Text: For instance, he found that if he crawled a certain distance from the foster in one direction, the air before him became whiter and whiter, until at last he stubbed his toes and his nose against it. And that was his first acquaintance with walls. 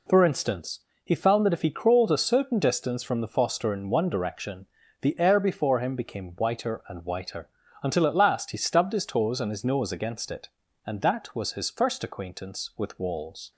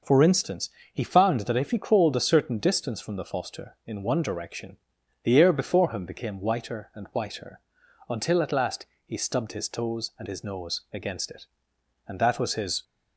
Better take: first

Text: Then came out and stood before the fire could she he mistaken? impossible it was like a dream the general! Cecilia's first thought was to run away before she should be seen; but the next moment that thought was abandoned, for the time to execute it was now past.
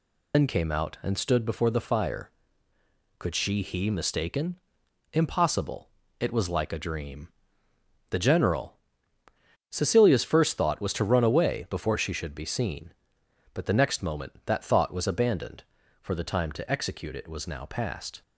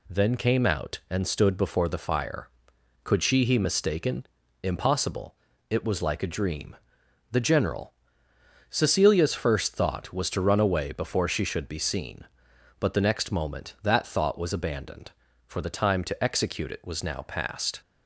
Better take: second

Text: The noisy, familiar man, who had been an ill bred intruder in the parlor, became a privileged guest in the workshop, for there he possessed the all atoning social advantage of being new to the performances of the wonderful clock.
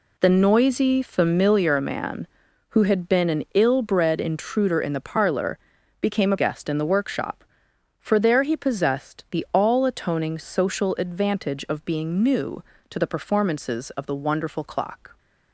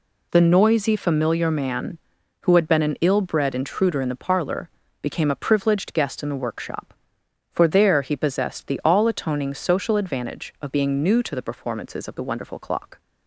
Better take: second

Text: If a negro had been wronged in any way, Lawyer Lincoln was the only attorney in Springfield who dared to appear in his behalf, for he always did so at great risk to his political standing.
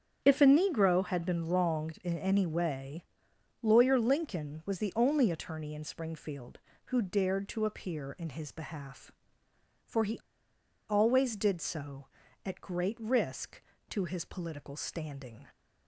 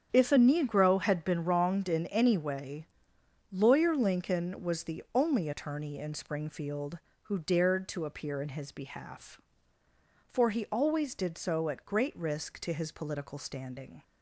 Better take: second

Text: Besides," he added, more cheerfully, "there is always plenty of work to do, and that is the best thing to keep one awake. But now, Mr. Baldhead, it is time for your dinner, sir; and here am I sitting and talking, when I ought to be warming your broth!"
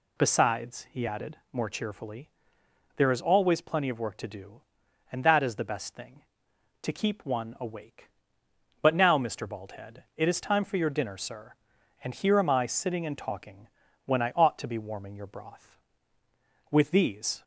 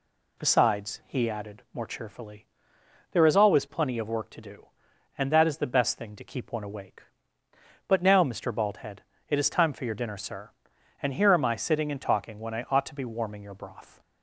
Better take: second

